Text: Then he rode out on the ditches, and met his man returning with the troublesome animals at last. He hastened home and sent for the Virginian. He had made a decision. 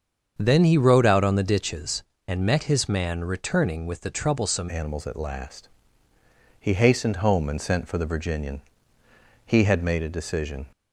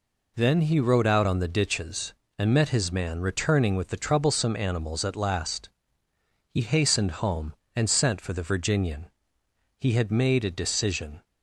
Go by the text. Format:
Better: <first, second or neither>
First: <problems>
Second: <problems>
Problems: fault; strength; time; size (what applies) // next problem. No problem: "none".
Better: second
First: starts louder than the rest; until 1.3 s; 7 dB // changes voice at "animals"; from 4.6 s on; 6.0 s long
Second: none